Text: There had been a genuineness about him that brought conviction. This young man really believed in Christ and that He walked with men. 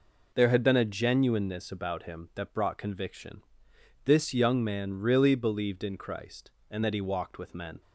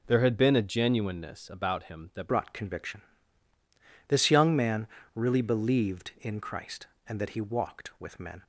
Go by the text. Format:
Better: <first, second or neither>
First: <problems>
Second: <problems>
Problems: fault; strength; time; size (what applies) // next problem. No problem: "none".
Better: first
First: none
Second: changes voice at "brought"; from 2.2 s on; 6.2 s long // pauses between "man" and "really"; slight; at 4.8 s; 0.28 s long